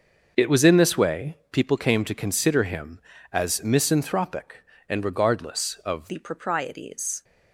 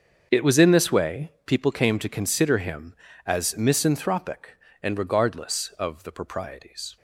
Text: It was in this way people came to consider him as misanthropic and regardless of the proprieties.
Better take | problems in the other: second | starts louder than the rest; noticeable; until 1.3 s; 6 dB; also in the second // changes voice at "the"; from 6.0 s on; 1.2 s long

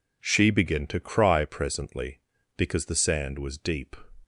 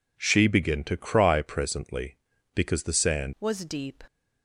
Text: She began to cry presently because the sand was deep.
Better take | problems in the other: first | changes voice at "was"; from 3.3 s on; 0.7 s long

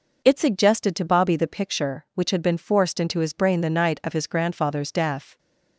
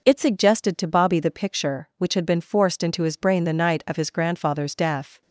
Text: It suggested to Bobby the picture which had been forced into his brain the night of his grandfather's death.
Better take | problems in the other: neither | none

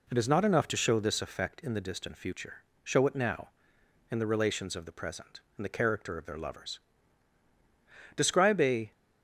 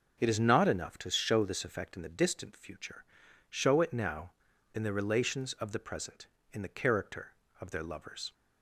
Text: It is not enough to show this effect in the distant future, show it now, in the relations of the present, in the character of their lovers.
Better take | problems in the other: second | goes on to say "Describe a"; noticeable; from 8.1 s on; 0.76 s long

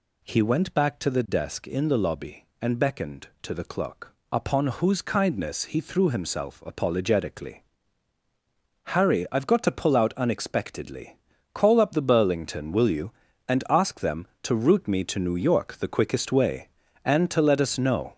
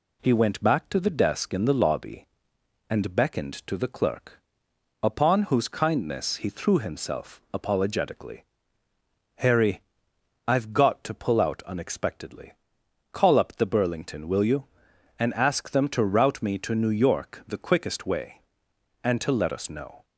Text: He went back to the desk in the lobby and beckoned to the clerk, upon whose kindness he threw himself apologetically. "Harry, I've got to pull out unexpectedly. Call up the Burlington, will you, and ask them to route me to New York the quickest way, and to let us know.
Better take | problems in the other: second | gets louder; noticeable; throughout; 5 dB

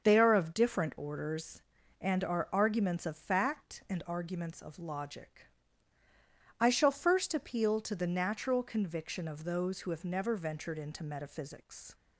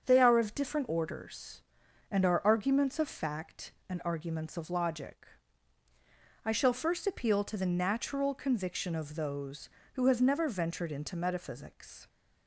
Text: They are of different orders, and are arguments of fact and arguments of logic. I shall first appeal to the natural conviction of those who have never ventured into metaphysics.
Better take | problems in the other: neither | starts louder than the rest; the same in both

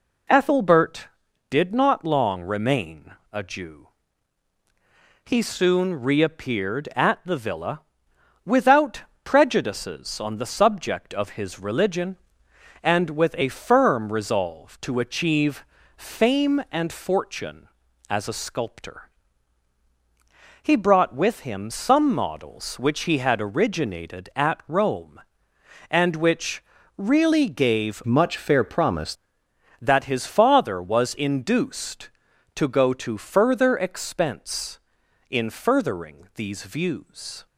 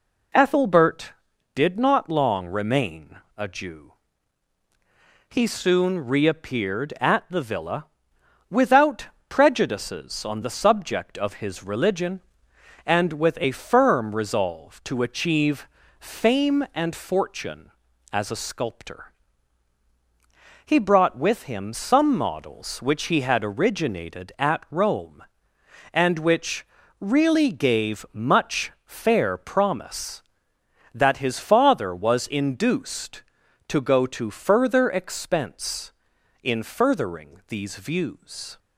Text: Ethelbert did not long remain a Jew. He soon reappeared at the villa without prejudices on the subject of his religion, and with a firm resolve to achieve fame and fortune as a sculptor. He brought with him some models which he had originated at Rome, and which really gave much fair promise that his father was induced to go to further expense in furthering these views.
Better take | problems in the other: second | pauses between "remain" and "a"; slight; at 3.1 s; 0.18 s long; slight in the second // pauses between "villa" and "without"; noticeable; at 7.7 s; 0.64 s long; noticeable in the second // pauses between "without" and "prejudices"; slight; at 9.0 s; 0.20 s long; slight in the second // pauses between "achieve" and "fame"; slight; at 15.6 s; 0.32 s long; slight in the second // pauses between "which" and "really"; slight; at 26.6 s; 0.36 s long; slight in the second // changes voice from "much" to "promise"; from 28.0 to 29.1 s; 1.1 s long

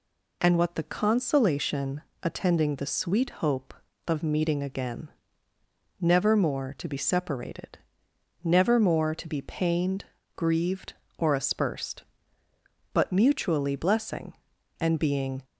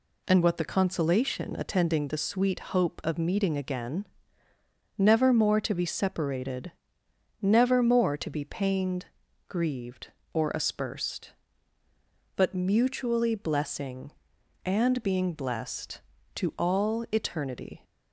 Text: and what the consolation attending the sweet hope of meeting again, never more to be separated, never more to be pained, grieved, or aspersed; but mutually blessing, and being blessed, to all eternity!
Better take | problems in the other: second | pauses between "consolation" and "attending"; slight; at 2.0 s; 0.22 s long // stops before "blessed to all eternity"; at 15.4 s

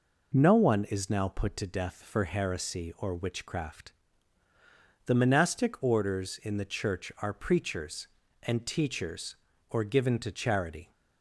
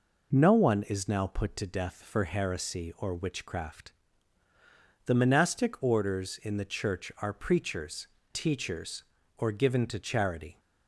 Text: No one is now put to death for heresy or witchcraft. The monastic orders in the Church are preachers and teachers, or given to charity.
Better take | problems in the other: first | skips "and"; at 8.2 s

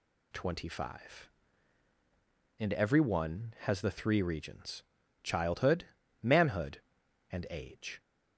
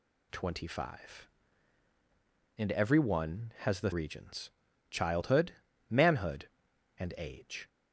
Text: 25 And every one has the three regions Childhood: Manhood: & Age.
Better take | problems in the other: first | skips "three"; at 3.9 s // pauses between "regions" and "Childhood"; at 4.4 s; 0.40 s long; also in the first

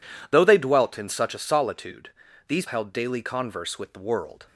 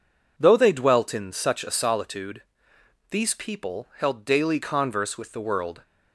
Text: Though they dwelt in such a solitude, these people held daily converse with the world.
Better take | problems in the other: second | skips "people"; at 2.6 s

